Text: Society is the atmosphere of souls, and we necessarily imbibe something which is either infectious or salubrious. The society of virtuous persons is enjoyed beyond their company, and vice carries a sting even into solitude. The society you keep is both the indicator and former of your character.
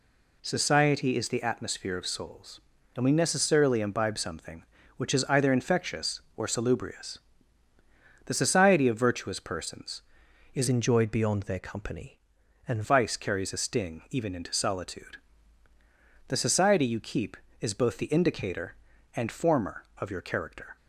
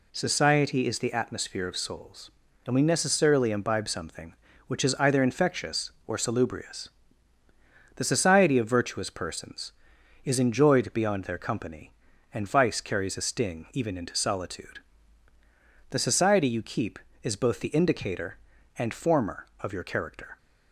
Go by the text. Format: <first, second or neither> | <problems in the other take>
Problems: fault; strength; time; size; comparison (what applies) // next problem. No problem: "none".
second | changes voice from "enjoyed" to "and"; from 10.6 to 12.8 s; 2.2 s long